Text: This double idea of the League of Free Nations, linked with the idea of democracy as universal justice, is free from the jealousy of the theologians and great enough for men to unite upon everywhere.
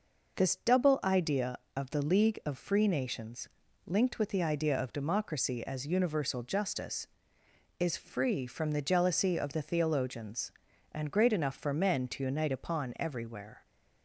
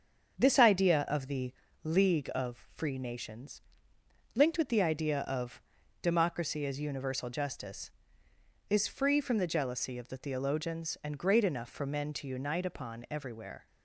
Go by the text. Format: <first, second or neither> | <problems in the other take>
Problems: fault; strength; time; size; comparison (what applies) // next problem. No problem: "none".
first | starts louder than the rest; until 1.4 s; 7 dB // skips "double"; at 0.5 s // pauses between "the" and "League"; slight; at 1.5 s; 0.28 s long // pauses between "of" and "democracy"; at 5.6 s; 0.40 s long